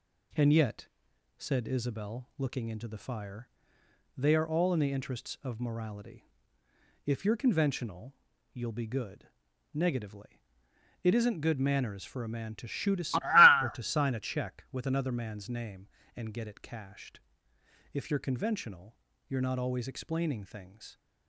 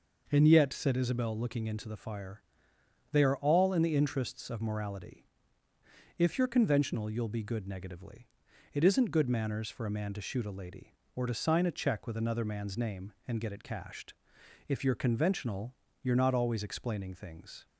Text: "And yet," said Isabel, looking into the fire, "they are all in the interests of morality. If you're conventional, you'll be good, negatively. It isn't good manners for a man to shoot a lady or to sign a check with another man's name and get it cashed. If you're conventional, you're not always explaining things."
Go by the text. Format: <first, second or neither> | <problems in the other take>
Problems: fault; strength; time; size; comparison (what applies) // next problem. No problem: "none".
second | skips "lady"; at 13.6 s